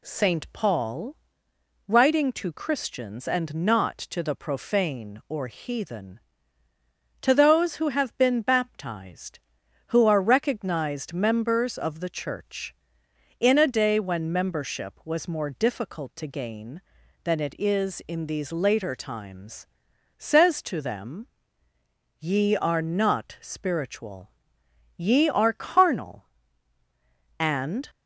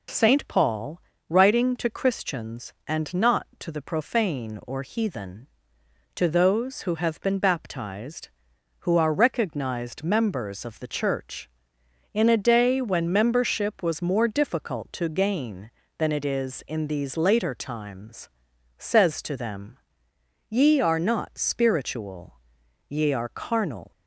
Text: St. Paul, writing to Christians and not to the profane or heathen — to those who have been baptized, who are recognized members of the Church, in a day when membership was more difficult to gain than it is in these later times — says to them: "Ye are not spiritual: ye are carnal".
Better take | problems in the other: second | goes on to say "And"; slight; from 27.3 s on; 0.48 s long

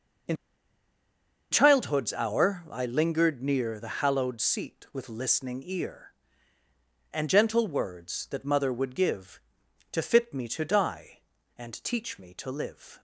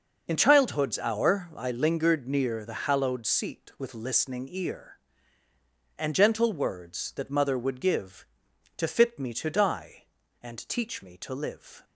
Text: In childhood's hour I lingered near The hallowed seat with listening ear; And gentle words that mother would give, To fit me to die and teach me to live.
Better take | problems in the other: second | pauses between "In" and "childhood's"; at 0.3 s; 1.1 s long

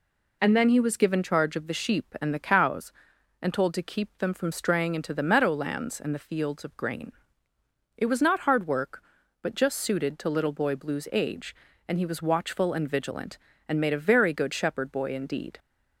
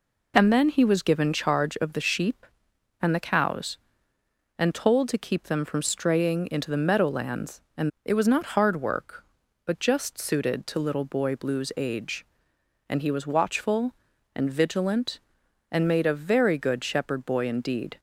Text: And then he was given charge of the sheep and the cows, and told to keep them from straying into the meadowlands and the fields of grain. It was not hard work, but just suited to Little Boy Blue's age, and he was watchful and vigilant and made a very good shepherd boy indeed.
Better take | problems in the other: first | skips "the fields of grain"; at 7.9 s

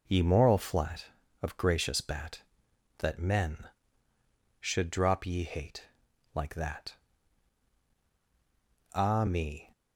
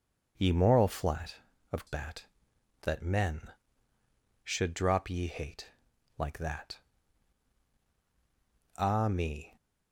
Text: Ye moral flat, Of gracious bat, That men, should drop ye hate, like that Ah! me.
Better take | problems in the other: first | skips "gracious"; at 1.8 s // pauses between "that" and "Ah"; strong; at 6.7 s; 2.0 s long; strong in the first

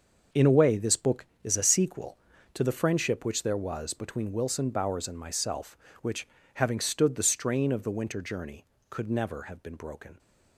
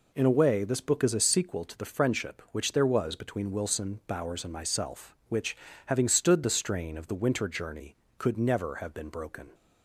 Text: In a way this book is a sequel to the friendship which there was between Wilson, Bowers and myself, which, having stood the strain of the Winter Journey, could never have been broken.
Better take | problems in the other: second | gets quieter; strong; throughout; 10 dB

